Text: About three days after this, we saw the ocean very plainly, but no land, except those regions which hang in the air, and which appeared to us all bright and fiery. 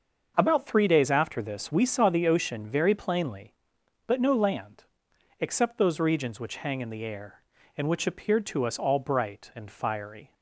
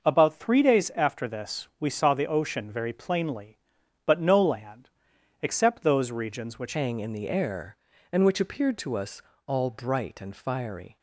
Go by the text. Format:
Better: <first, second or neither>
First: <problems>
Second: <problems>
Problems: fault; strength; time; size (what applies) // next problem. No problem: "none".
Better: first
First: starts louder than the rest; until 1.3 s; 6.5 dB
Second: starts louder than the rest; noticeable; until 1.0 s; 6 dB // changes voice at "hang"; from 6.7 s on; 4.2 s long // pauses between "us" and "all"; slight; at 9.2 s; 0.24 s long